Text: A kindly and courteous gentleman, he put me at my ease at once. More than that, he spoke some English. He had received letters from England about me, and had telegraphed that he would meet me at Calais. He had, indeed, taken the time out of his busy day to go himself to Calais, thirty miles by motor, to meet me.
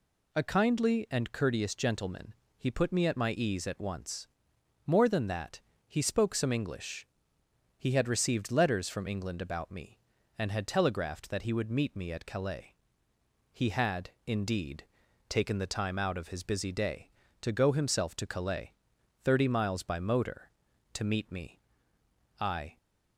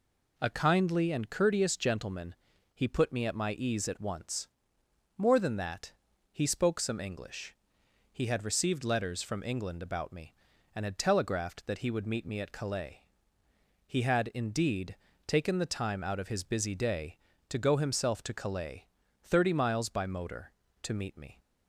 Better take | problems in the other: second | goes on to say "I"; slight; from 22.3 s on; 0.38 s long

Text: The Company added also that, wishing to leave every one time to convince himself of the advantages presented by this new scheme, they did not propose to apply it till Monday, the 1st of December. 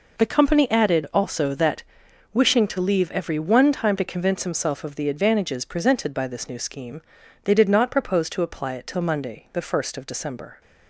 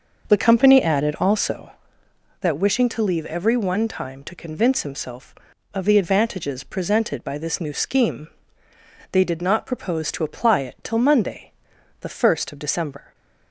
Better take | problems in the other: first | starts louder than the rest; until 1.7 s; 6 dB

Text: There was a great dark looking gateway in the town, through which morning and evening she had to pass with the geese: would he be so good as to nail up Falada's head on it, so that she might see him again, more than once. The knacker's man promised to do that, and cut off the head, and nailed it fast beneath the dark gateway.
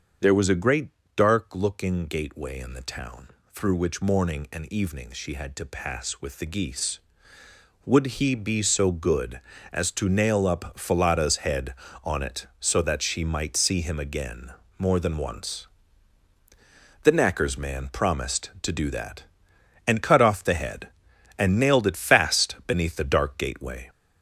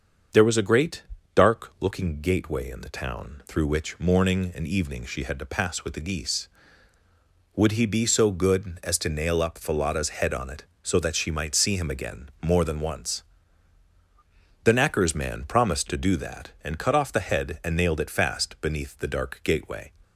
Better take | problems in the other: second | gets louder; noticeable; throughout; 4.5 dB // starts louder than the rest; until 1.4 s; 7 dB; also in the second // pauses between "great" and "dark"; slight; at 0.8 s; 0.26 s long; slight in the second

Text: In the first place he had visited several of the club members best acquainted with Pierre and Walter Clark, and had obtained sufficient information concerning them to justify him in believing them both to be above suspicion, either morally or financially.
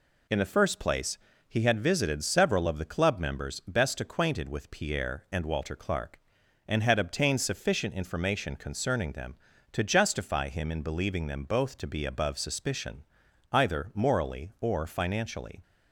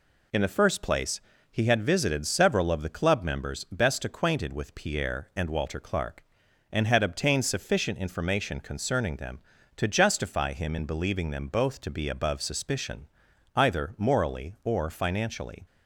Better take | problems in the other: neither | pauses between "place" and "he"; slight; the same in both

